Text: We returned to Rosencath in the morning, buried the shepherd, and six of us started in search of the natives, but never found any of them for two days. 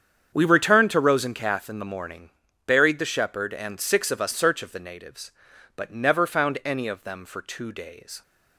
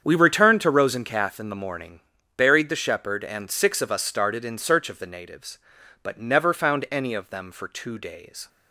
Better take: second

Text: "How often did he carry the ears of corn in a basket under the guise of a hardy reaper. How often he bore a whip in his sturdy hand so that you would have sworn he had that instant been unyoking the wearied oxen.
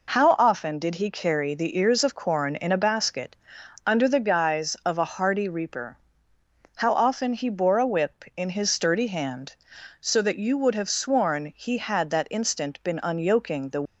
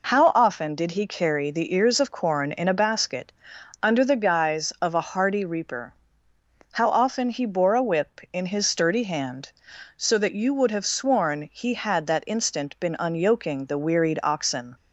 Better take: second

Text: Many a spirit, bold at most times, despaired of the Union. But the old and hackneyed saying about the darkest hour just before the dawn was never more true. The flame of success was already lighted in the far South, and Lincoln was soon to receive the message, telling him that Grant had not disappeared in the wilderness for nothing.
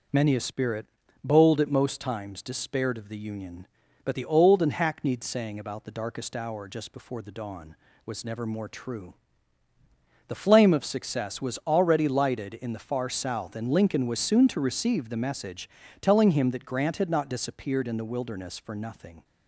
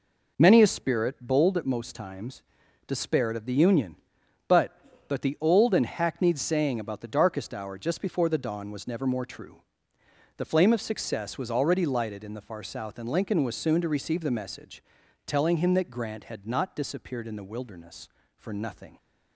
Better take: first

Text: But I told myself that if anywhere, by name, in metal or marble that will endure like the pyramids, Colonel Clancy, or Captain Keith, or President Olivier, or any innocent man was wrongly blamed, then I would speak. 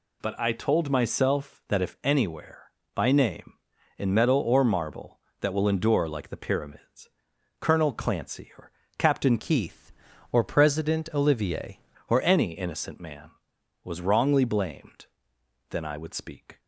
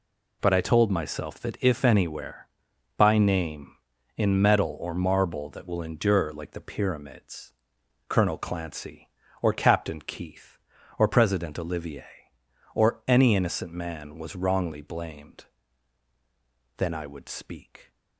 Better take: second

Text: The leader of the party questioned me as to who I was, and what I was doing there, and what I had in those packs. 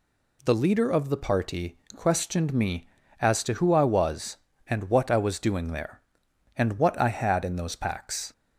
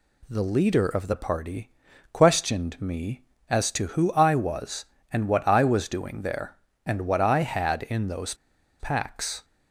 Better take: first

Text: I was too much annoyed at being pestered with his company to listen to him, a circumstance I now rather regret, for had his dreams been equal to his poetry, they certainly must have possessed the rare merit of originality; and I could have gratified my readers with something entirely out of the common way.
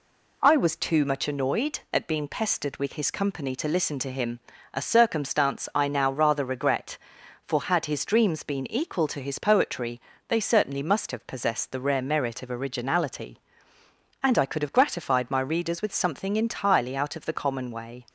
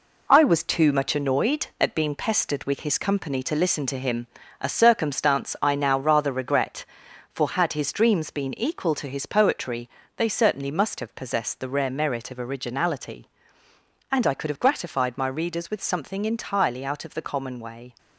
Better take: first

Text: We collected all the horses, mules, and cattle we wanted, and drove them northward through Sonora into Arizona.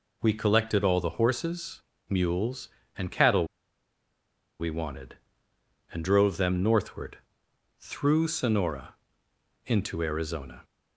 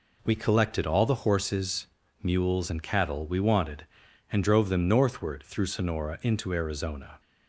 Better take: second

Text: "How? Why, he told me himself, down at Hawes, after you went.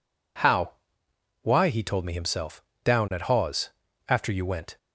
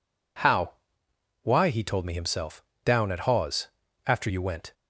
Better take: neither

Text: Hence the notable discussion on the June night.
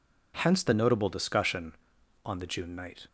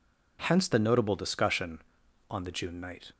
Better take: neither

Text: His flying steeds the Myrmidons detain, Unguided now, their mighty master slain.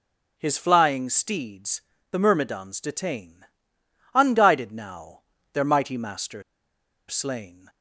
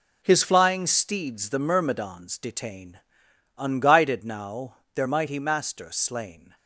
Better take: second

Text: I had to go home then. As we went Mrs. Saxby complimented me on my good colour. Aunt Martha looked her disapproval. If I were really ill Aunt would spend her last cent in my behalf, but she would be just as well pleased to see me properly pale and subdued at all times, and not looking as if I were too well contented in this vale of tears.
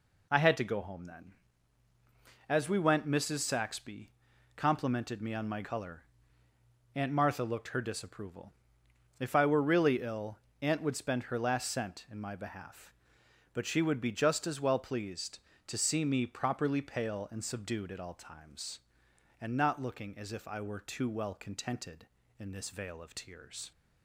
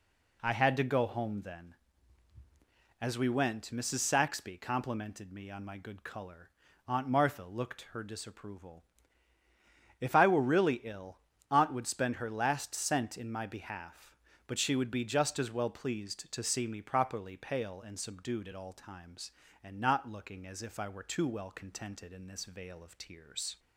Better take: second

